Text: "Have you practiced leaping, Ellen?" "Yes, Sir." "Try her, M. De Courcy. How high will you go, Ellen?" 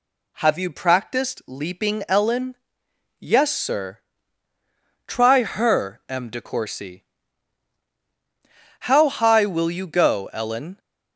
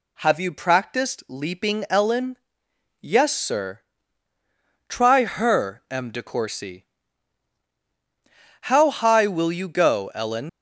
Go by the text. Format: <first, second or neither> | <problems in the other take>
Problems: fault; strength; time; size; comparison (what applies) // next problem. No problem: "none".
first | leaves "Ellen" unfinished; at 10.4 s; 100 ms